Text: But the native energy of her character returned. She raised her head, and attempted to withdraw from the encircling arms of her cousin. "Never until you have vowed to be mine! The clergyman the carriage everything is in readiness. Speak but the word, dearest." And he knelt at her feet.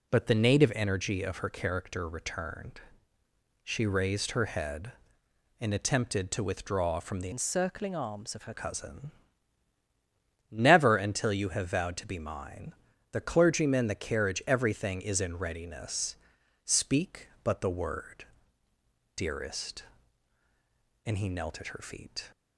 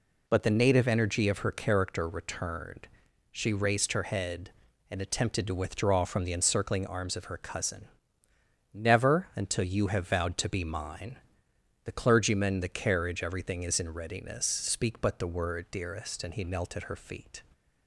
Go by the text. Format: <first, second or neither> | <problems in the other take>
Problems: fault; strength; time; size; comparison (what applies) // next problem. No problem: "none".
second | changes voice from "encircling" to "her"; from 7.3 to 8.5 s; 1.2 s long